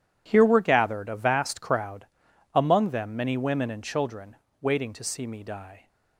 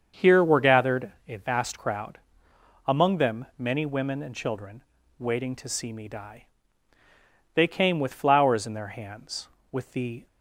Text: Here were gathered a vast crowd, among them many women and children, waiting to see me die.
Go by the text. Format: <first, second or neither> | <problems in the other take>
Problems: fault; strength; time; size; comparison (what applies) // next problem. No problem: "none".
first | starts louder than the rest; until 1.3 s; 7 dB // pauses between "gathered" and "a"; slight; at 1.1 s; 0.16 s long // goes on to say "They came with flowers in their hands with the"; strong; from 7.5 s on; 2.7 s long